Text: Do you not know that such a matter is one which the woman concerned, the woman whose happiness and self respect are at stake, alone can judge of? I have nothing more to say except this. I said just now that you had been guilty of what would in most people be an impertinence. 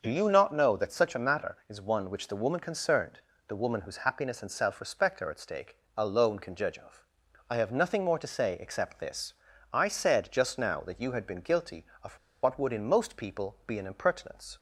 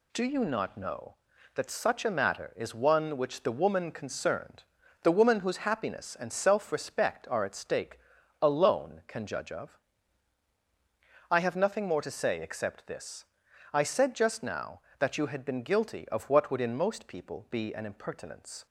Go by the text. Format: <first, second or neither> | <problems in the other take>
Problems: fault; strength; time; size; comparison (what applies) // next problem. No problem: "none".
second | starts louder than the rest; until 1.0 s; 6.5 dB // pauses between "of" and "what"; slight; at 12.1 s; 0.25 s long